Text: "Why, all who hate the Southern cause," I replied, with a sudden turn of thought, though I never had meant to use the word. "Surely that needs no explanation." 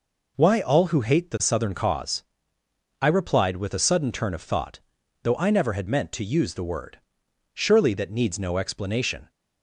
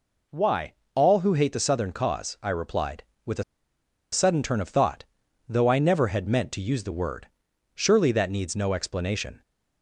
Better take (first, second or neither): first